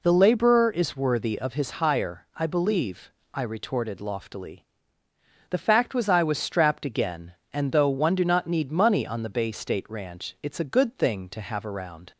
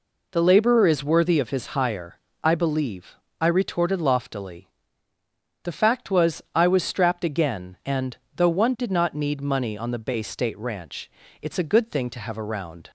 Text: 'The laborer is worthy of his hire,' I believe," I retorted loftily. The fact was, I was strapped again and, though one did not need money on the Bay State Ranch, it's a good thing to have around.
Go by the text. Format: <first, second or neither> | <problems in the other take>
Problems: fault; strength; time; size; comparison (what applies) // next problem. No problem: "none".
second | says "do" for "did"; at 8.1 s